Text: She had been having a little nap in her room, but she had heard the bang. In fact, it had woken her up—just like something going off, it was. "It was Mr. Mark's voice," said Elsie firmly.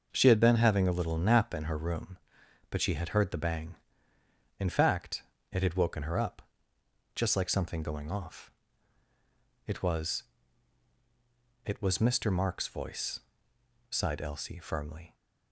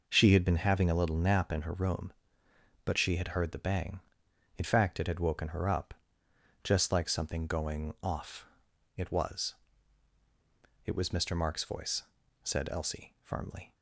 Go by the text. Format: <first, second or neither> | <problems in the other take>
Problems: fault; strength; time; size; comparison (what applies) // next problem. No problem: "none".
second | starts louder than the rest; until 1.1 s; 6 dB // says "sighed" for "said"; at 13.8 s